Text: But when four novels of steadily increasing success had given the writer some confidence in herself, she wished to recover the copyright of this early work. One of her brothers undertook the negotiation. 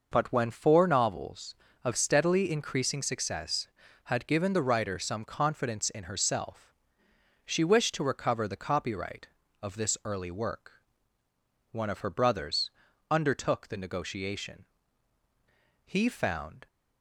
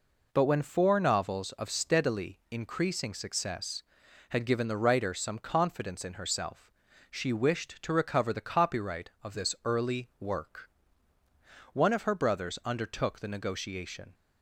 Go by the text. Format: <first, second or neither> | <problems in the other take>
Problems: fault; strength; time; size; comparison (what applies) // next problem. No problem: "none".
second | pauses between "brothers" and "undertook"; at 12.7 s; 0.40 s long // goes on to say "He found"; noticeable; from 15.8 s on; 0.80 s long